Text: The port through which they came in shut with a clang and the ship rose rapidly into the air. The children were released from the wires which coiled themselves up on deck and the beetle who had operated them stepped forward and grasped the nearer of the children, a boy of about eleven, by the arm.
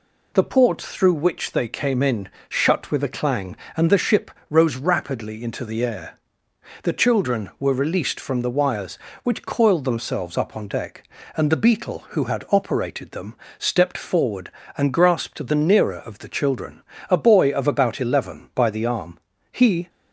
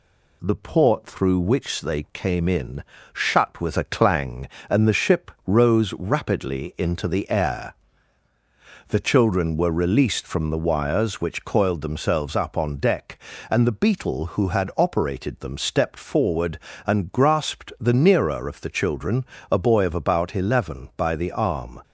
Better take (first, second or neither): second